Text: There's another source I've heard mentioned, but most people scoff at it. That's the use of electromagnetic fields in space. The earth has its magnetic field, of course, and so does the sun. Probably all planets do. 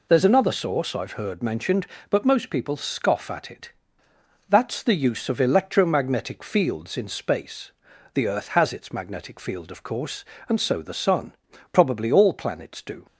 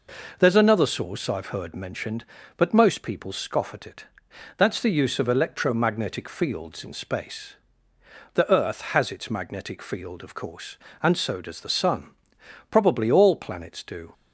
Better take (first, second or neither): second